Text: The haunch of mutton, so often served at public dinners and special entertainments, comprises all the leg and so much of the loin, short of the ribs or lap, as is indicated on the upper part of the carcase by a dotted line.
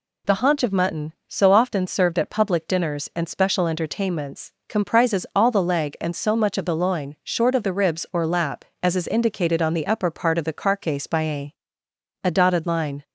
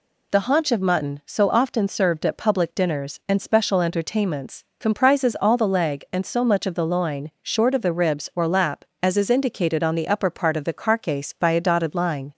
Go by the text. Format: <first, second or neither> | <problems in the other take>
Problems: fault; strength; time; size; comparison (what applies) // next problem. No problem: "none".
second | says "a" twice; at 12.2 s